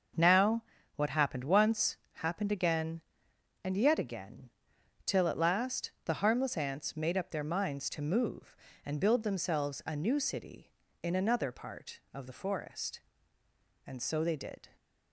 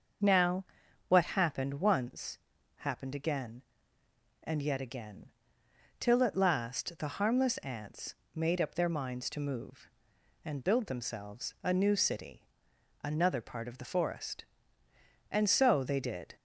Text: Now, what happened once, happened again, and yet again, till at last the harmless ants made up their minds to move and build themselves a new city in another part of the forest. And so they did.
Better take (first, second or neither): first